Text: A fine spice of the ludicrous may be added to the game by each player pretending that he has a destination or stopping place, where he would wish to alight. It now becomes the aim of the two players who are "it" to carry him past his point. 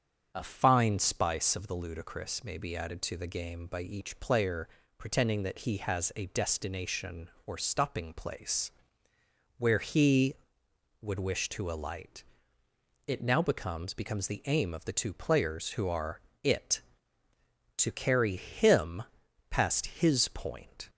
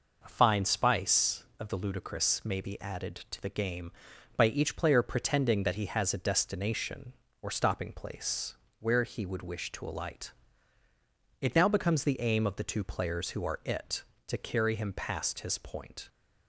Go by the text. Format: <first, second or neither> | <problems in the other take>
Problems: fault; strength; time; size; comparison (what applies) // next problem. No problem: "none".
second | starts louder than the rest; until 1.3 s; 7 dB // pauses between "player" and "pretending"; slight; at 4.6 s; 0.32 s long // says "becomes" twice; at 13.9 s // pauses between "are" and "it"; slight; at 16.1 s; 0.24 s long // pauses between "him" and "past"; noticeable; at 19.0 s; 0.48 s long